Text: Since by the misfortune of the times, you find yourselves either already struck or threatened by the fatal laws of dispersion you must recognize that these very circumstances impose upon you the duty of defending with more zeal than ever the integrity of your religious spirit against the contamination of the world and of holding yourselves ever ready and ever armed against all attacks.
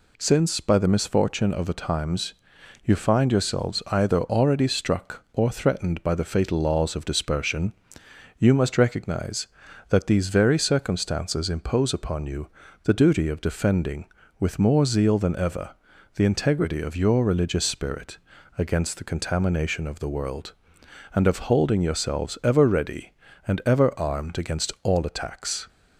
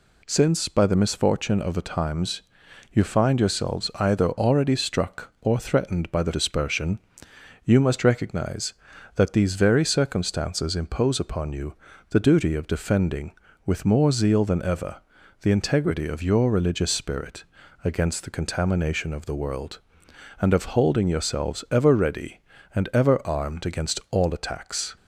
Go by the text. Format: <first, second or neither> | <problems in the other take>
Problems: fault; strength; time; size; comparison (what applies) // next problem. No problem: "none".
first | skips "fatal laws of"; at 6.3 s // pauses between "dispersion" and "you"; noticeable; at 6.9 s; 0.64 s long; noticeable in the first // pauses between "you" and "the"; slight; at 11.7 s; 0.34 s long; slight in the first // pauses between "ever" and "the"; at 14.9 s; 0.42 s long; also in the first // pauses between "spirit" and "against"; at 17.4 s; 0.40 s long; also in the first